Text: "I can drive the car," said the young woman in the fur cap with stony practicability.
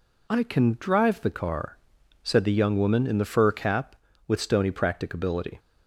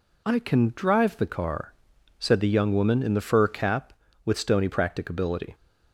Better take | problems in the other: neither | none

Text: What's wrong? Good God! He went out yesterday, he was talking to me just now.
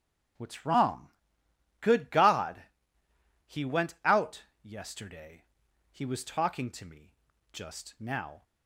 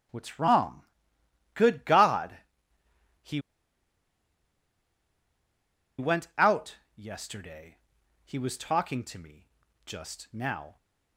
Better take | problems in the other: first | starts louder than the rest; strong; until 1.8 s; 8.5 dB; strong in the first // pauses between "He" and "went"; strong; at 3.3 s; 2.5 s long // pauses between "out" and "yesterday"; slight; at 6.7 s; 0.22 s long; slight in the first // pauses between "me" and "just"; at 9.4 s; 0.38 s long; also in the first

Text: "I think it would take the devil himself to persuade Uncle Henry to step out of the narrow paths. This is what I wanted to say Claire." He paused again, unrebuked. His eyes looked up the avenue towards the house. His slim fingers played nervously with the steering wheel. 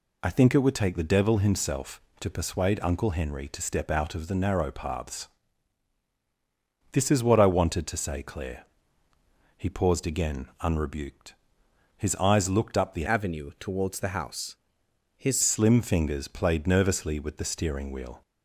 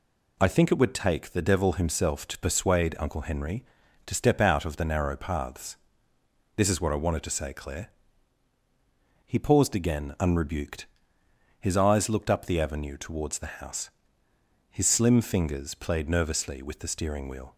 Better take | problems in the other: second | changes voice from "avenue" to "His"; from 13.0 to 15.3 s; 2.3 s long

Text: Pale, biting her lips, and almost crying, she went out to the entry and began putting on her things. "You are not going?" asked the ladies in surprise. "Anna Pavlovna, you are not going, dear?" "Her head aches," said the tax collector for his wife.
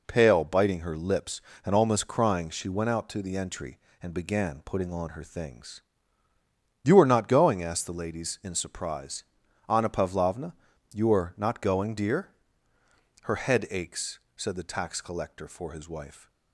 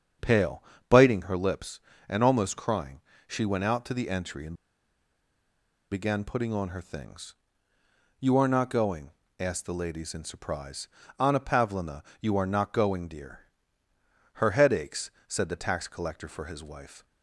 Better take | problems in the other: first | starts louder than the rest; strong; until 1.4 s; 7.5 dB // pauses between "and" and "began"; strong; at 4.5 s; 1.3 s long

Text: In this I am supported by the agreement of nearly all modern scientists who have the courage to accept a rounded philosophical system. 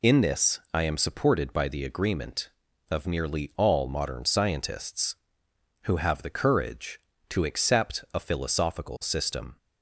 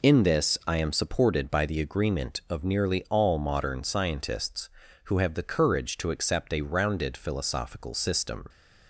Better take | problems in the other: second | skips "rounded"; at 8.1 s

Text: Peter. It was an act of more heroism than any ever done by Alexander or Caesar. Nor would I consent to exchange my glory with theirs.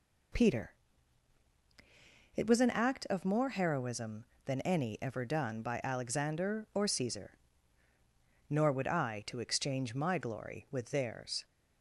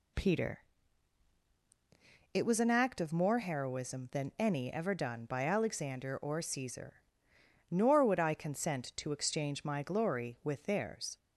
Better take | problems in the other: second | skips "consent"; at 9.2 s

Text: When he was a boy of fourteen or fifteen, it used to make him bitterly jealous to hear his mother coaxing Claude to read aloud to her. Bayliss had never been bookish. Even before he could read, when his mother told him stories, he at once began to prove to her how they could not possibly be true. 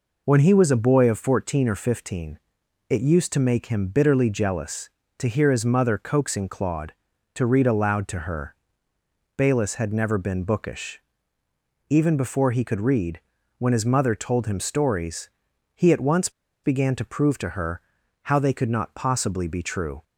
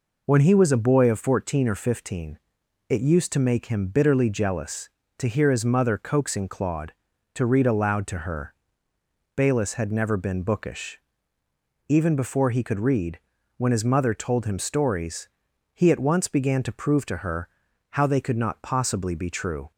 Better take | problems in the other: second | pauses between "once" and "began"; slight; at 16.2 s; 0.33 s long // pauses between "her" and "how"; at 17.8 s; 0.42 s long; also in the second

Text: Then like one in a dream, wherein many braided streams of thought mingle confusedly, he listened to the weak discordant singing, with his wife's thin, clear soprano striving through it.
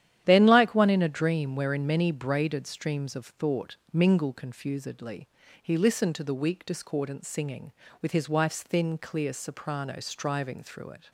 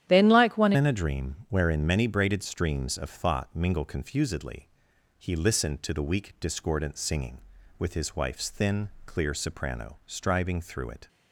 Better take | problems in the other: first | starts louder than the rest; strong; until 1.1 s; 10.5 dB; strong in the first // changes voice at "in"; from 0.7 s on; 10.3 s long

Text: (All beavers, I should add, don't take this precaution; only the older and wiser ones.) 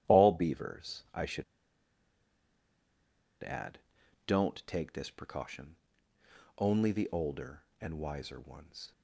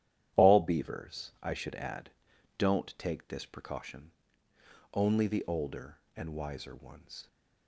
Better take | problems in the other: second | starts louder than the rest; strong; until 1.1 s; 11.5 dB; strong in the second // pauses between "should" and "add"; strong; at 1.4 s; 1.9 s long

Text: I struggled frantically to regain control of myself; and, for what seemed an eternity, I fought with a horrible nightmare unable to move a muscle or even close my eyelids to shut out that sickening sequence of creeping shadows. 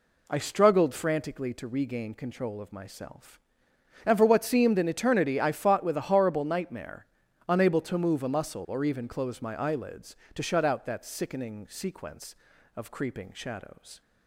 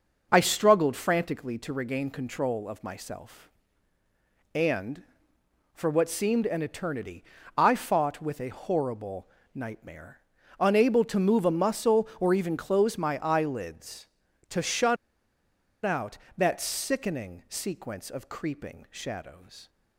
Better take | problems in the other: first | pauses between "horrible" and "nightmare"; slight; at 9.2 s; 0.26 s long // pauses between "nightmare" and "unable"; slight; at 10.2 s; 0.36 s long; also in the first // pauses between "shut" and "out"; noticeable; at 14.9 s; 0.88 s long

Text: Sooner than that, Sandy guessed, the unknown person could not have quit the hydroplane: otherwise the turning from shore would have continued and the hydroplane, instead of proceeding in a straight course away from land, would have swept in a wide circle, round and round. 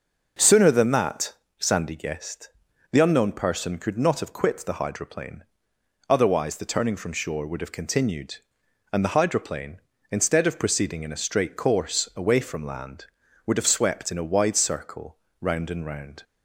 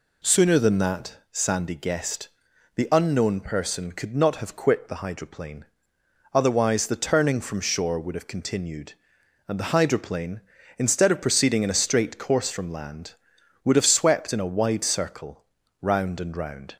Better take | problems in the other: first | skips "away"; at 12.5 s

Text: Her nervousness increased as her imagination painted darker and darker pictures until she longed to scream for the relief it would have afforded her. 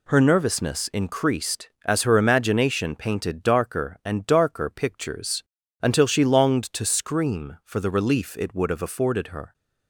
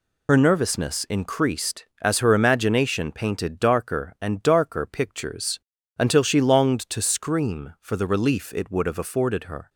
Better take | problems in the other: first | loses the start of "Her"; at 0.2 s; 55 ms // pauses between "pictures" and "until"; at 5.5 s; 0.40 s long; also in the first

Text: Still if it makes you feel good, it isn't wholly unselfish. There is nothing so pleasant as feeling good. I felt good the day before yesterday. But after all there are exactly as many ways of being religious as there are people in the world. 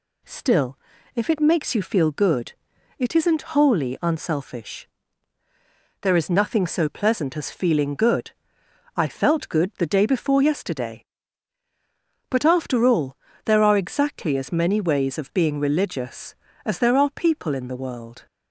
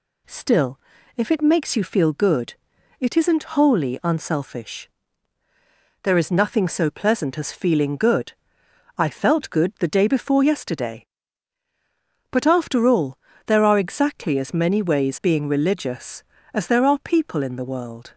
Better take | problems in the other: first | pauses between "Still" and "if"; at 0.7 s; 0.38 s long; also in the first // pauses between "all" and "there"; slight; at 13.1 s; 0.30 s long; slight in the first // skips "of"; at 15.2 s

